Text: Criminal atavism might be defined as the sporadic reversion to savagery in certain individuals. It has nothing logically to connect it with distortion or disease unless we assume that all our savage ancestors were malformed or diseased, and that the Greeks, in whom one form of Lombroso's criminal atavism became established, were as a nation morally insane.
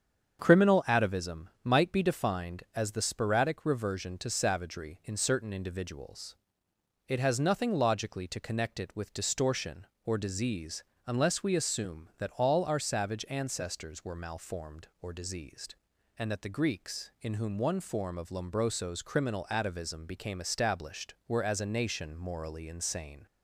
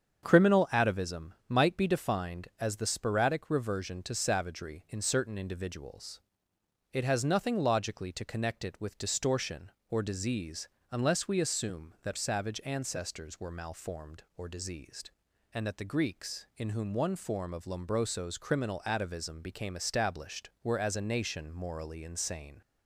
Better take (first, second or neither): first